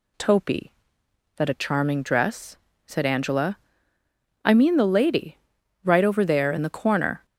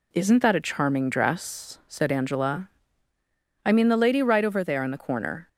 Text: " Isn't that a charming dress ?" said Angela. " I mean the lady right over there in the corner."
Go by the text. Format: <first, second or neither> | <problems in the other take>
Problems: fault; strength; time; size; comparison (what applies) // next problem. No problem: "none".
second | says "Topi" for "Isn't"; at 0.1 s // pauses between "lady" and "right"; at 5.3 s; 0.44 s long